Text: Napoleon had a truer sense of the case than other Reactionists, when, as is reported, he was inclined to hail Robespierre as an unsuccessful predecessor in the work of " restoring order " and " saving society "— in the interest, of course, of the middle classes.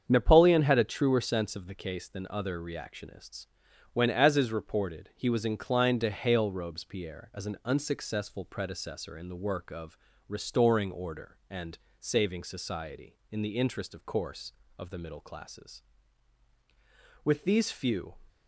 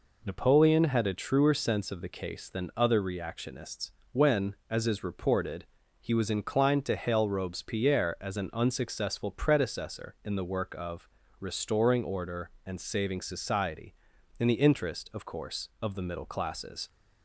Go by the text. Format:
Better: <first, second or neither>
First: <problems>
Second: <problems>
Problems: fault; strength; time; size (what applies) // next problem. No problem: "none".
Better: second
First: starts louder than the rest; strong; until 1.0 s; 7.5 dB // goes on to say "With these few"; noticeable; from 17.2 s on; 0.90 s long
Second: none